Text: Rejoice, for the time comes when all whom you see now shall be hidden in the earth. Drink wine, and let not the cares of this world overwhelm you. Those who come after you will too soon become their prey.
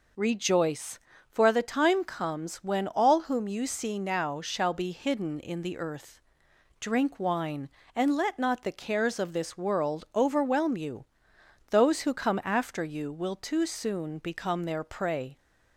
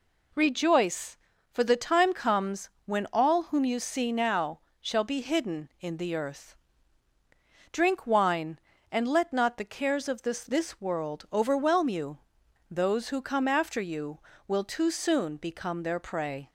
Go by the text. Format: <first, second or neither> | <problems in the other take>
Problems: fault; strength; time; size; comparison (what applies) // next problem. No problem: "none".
first | pauses between "comes" and "when"; slight; at 2.7 s; 0.16 s long // pauses between "now" and "shall"; slight; at 4.6 s; 0.20 s long // says "this" twice; at 10.4 s